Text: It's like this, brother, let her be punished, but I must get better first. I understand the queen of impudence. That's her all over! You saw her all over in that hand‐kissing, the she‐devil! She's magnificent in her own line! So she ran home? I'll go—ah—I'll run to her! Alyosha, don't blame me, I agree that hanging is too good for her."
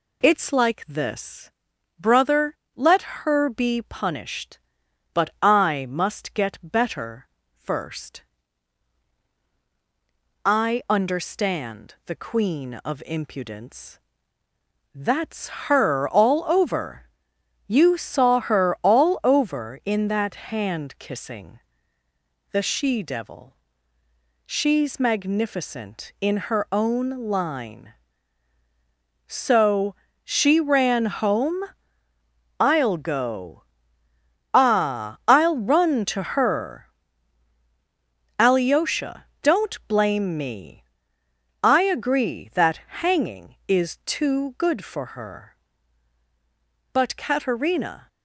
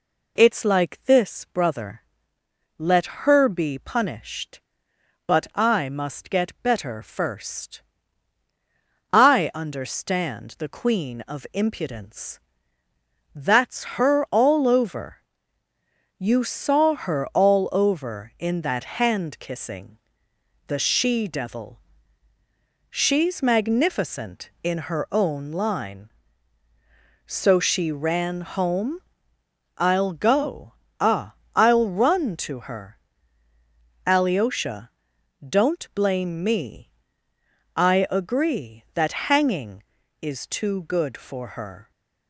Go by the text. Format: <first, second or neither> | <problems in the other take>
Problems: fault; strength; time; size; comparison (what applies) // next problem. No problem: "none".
second | pauses between "better" and "first"; slight; at 7.2 s; 0.32 s long // pauses between "That's" and "her"; slight; at 15.4 s; 0.18 s long // pauses between "own" and "line"; slight; at 27.0 s; 0.18 s long // pauses between "So" and "she"; slight; at 29.9 s; 0.28 s long // pauses between "that" and "hanging"; slight; at 42.7 s; 0.22 s long // goes on to say "But Katerina"; noticeable; from 46.9 s on; 1.1 s long